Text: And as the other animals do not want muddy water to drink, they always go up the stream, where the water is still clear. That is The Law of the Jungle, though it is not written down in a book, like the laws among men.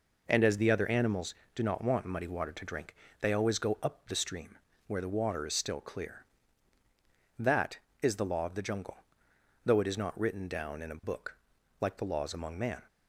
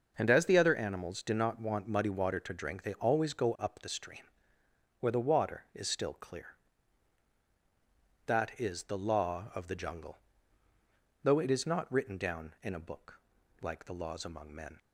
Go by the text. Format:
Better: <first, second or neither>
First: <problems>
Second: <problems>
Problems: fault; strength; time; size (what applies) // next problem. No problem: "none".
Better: second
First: says "man" for "men"; at 12.5 s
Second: none